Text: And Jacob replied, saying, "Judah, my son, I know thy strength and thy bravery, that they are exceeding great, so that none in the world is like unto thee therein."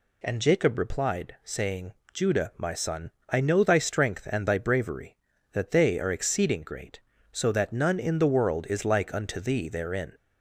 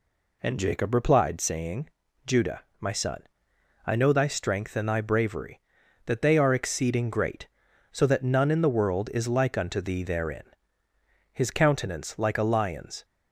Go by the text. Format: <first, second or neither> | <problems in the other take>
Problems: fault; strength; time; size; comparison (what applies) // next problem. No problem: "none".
first | goes on to say "His countenance like a lion's"; strong; from 11.3 s on; 1.7 s long